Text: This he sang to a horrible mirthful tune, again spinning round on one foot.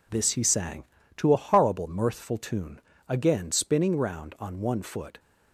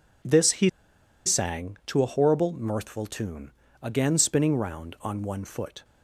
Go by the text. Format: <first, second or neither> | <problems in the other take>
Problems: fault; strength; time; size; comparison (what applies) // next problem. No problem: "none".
first | pauses between "he" and "sang"; noticeable; at 0.6 s; 0.57 s long